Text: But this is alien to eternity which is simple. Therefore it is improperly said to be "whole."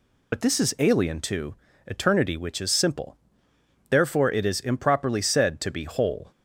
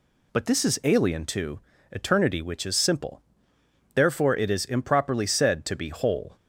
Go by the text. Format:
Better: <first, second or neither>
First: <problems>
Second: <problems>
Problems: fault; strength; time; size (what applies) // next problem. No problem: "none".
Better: second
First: loses the start of "But"; at 0.3 s; 55 ms // pauses between "to" and "eternity"; slight; at 1.5 s; 0.32 s long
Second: pauses between "to" and "eternity"; slight; at 1.5 s; 0.32 s long